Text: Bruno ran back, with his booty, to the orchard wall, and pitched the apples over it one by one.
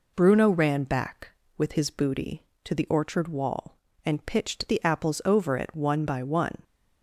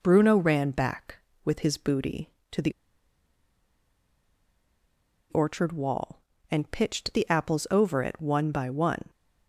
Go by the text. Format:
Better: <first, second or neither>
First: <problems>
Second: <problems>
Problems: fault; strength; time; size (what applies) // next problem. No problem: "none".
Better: first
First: none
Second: pauses between "the" and "orchard"; strong; at 2.7 s; 2.5 s long